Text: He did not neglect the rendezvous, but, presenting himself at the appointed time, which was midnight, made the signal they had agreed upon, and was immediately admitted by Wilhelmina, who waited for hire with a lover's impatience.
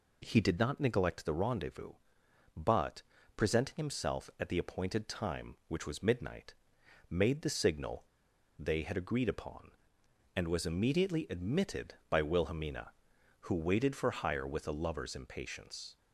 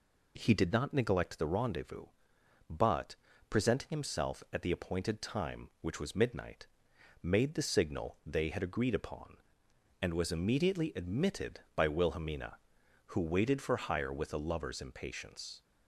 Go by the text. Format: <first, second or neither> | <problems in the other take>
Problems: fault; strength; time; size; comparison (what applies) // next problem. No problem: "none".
second | pauses between "signal" and "they"; noticeable; at 8.0 s; 0.53 s long